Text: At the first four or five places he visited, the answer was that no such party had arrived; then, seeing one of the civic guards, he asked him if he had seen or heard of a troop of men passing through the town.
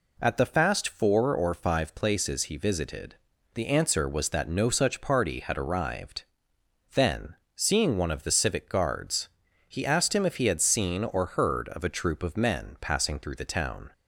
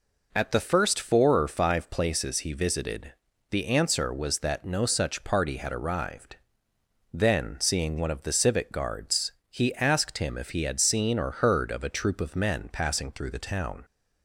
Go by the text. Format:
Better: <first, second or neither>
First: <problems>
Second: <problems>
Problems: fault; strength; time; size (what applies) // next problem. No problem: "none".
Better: second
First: says "fast" for "first"; at 0.4 s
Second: none